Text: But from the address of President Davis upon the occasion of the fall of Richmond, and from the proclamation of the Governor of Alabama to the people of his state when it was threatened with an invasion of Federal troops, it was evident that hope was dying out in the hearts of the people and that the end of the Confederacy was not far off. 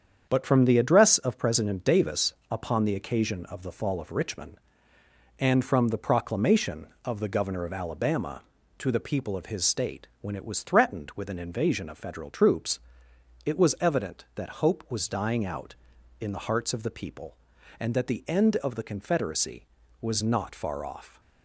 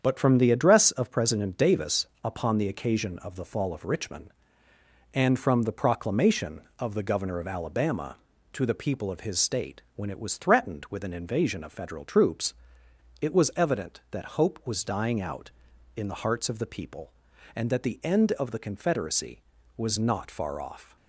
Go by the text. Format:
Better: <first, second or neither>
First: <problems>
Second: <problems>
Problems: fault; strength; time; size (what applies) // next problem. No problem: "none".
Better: neither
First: starts louder than the rest; strong; until 1.3 s; 7.5 dB // pauses between "Davis" and "upon"; slight; at 2.3 s; 0.18 s long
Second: starts louder than the rest; strong; until 1.0 s; 7.5 dB // pauses between "Davis" and "upon"; slight; at 2.0 s; 0.18 s long